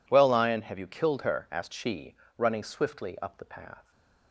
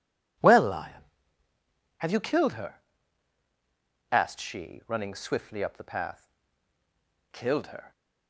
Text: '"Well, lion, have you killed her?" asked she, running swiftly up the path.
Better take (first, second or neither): first